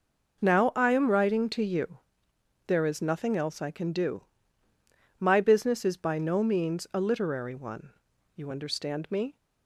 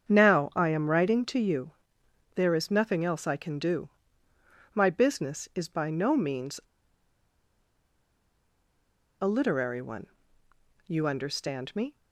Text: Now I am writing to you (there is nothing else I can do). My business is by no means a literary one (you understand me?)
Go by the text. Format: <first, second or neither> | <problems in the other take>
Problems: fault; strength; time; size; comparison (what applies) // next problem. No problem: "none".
first | starts louder than the rest; strong; until 1.1 s; 7.5 dB // pauses between "means" and "a"; strong; at 6.6 s; 2.6 s long